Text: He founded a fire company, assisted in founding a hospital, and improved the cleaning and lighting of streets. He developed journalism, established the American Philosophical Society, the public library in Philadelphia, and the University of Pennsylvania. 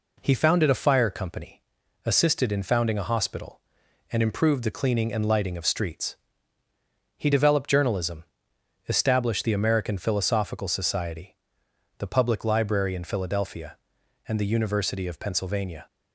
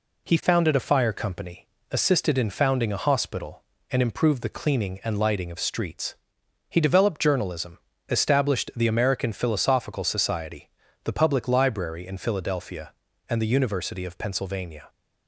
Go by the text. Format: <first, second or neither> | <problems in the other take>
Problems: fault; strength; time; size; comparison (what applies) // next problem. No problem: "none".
neither | none